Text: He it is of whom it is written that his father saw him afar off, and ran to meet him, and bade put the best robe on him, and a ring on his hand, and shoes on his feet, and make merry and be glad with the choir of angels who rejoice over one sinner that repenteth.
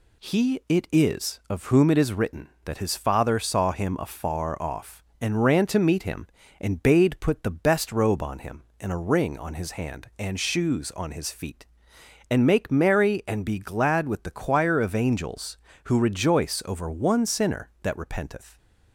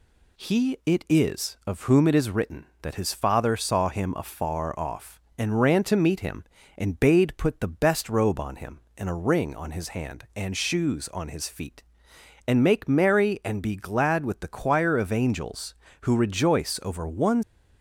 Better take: first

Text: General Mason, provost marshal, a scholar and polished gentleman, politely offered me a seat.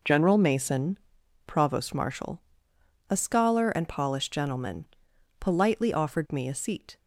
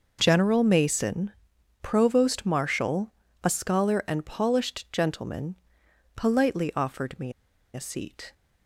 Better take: first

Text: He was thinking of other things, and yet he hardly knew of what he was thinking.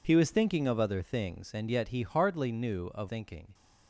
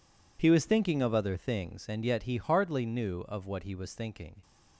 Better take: second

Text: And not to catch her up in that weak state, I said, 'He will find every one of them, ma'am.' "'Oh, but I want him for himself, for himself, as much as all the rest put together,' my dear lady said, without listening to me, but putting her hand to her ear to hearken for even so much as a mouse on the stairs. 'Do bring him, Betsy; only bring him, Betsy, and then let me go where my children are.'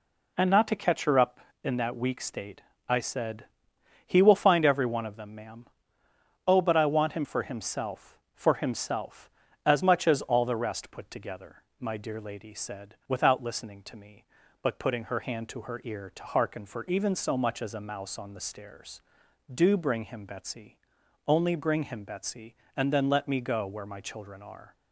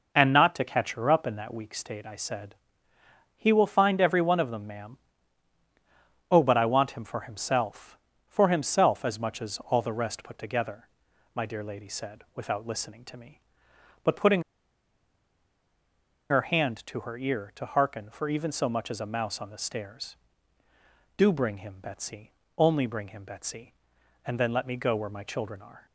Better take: first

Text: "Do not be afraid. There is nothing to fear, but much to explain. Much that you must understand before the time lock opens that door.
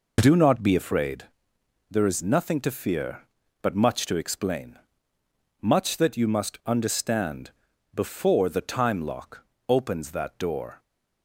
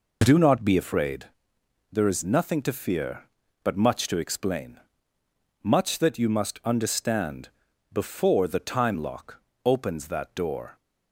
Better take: neither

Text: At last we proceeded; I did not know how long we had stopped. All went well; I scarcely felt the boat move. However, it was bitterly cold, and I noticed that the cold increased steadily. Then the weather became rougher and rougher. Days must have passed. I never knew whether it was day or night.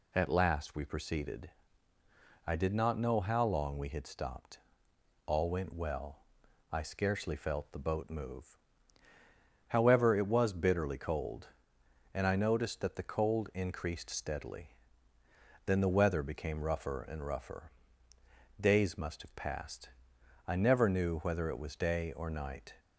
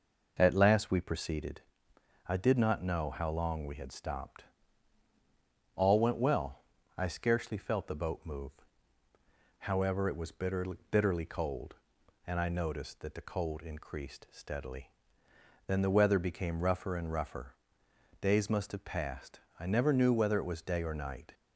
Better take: first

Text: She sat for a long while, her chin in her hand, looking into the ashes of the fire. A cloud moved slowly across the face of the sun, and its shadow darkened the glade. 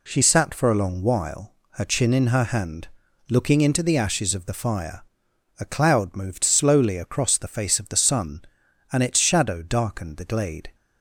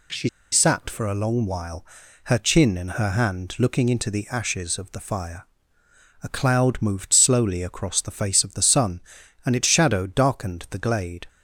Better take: first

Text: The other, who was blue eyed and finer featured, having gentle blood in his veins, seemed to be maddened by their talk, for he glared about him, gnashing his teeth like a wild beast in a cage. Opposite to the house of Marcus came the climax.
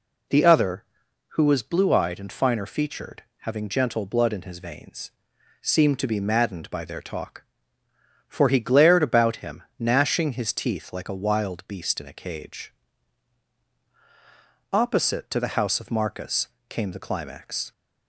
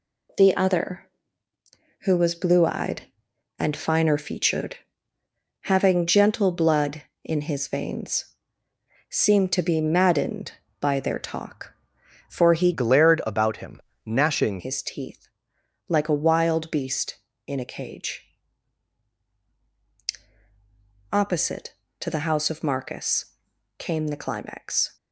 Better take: first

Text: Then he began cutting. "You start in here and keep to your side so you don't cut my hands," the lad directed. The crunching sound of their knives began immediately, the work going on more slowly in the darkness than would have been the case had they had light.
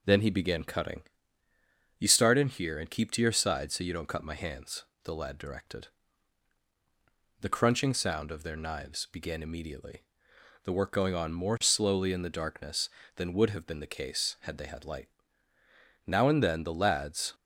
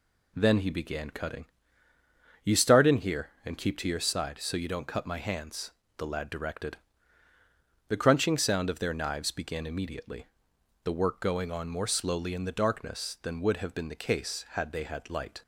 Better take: second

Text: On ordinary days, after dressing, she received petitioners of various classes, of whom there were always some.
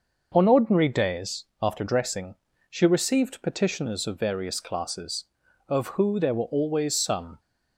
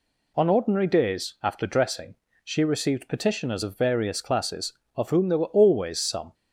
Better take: second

